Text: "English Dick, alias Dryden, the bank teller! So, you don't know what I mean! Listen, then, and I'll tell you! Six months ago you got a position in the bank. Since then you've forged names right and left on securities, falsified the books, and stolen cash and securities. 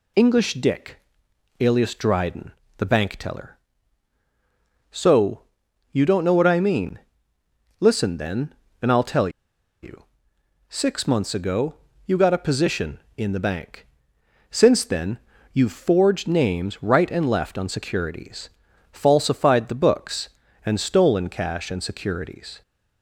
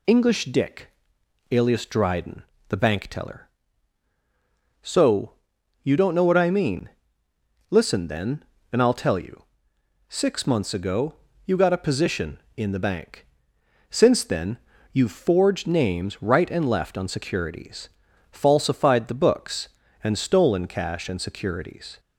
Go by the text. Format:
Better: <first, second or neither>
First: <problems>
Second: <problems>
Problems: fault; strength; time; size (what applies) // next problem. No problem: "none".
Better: second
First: pauses between "tell" and "you"; noticeable; at 9.2 s; 0.53 s long // pauses between "ago" and "you"; slight; at 11.7 s; 0.32 s long // pauses between "then" and "you've"; slight; at 15.1 s; 0.34 s long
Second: pauses between "ago" and "you"; slight; at 11.1 s; 0.32 s long // pauses between "then" and "you've"; slight; at 14.5 s; 0.34 s long